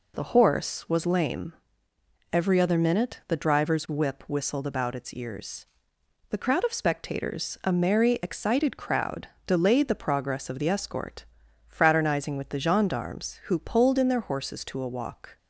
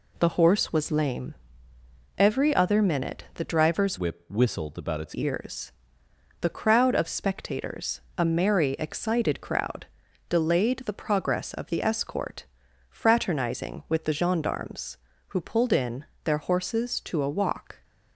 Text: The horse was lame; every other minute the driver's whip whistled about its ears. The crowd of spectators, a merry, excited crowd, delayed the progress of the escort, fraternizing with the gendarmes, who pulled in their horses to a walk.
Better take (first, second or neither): first